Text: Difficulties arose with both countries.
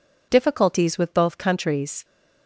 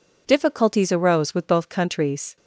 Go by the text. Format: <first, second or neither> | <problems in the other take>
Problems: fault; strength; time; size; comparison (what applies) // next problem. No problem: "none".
second | skips "arose"; at 0.9 s